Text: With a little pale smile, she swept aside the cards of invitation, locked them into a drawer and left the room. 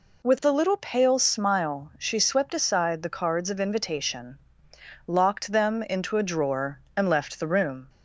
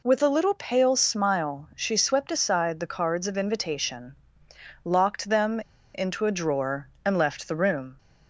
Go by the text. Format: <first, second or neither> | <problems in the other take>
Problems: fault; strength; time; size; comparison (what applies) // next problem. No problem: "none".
first | pauses between "them" and "into"; slight; at 5.6 s; 0.33 s long